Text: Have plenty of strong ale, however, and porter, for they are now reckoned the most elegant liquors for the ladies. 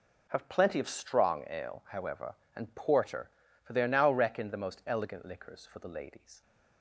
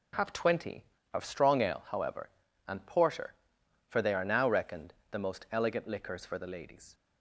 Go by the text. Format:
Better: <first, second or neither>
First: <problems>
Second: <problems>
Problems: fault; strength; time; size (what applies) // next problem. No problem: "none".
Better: first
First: none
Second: says "twenty" for "plenty"; at 0.3 s // pauses between "reckoned" and "the"; slight; at 4.9 s; 0.16 s long